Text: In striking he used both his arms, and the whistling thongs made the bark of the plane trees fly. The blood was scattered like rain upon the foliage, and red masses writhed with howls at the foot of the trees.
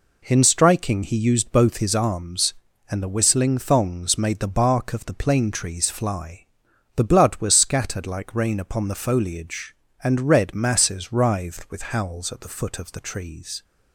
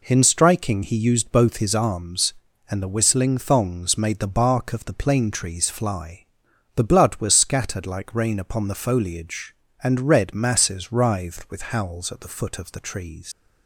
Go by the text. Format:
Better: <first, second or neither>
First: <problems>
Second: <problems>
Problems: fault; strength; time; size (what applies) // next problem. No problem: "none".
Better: first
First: none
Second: leaves "trees" unfinished; at 13.3 s; 115 ms